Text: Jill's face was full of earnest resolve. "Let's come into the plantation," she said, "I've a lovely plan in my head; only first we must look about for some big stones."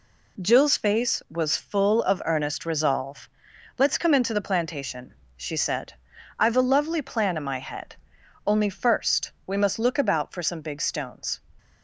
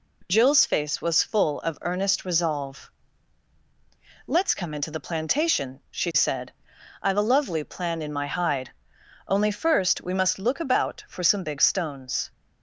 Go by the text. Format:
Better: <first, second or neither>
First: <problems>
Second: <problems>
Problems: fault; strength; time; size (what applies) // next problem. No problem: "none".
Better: first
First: none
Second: says "hide" for "head"; at 8.2 s